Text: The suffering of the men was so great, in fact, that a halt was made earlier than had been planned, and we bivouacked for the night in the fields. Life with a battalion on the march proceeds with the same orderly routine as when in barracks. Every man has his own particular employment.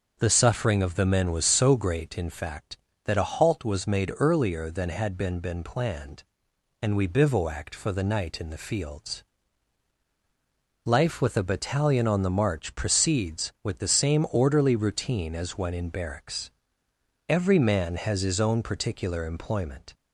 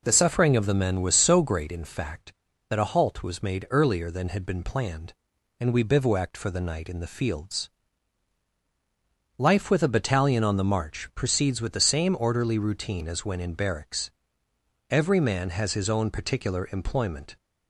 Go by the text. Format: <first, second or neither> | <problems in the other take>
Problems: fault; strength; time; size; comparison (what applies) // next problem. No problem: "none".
second | starts louder than the rest; until 1.2 s; 6.5 dB // says "been" twice; at 5.3 s